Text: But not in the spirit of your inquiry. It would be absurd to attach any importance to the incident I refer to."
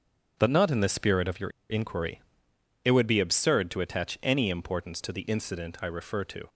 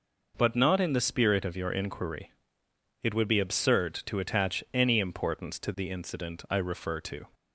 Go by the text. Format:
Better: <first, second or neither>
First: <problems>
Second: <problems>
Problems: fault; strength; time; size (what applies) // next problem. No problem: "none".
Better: second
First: starts louder than the rest; strong; until 1.3 s; 7.5 dB // pauses between "your" and "inquiry"; slight; at 1.4 s; 0.20 s long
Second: none